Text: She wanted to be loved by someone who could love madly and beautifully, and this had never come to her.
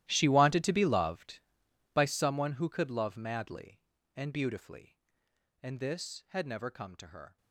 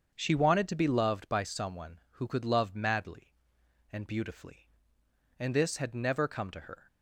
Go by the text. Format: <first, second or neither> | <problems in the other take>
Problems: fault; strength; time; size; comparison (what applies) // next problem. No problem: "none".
second | gets quieter; strong; throughout; 18.5 dB // starts louder than the rest; strong; until 1.0 s; 14 dB; also in the second